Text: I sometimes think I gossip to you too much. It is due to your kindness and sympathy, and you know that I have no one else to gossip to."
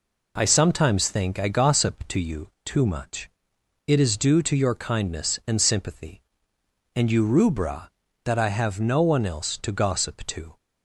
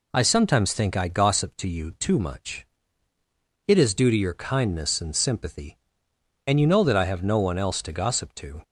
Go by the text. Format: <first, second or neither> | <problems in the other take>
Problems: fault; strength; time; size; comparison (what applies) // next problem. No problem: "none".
second | pauses between "you" and "too"; slight; at 2.5 s; 0.16 s long // says "rubra" for "know"; at 7.2 s